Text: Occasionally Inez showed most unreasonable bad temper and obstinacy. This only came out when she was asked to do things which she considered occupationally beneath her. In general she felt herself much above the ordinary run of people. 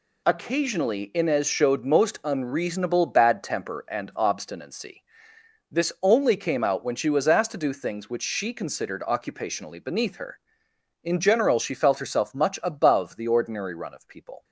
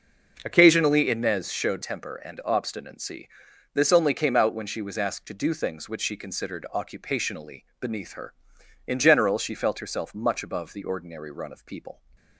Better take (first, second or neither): first